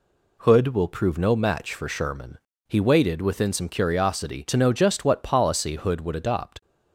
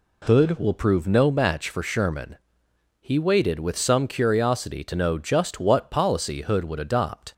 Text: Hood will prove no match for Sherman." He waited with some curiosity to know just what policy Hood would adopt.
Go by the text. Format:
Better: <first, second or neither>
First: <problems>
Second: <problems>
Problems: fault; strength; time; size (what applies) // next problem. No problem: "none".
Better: second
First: says "within" for "with"; at 3.2 s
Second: none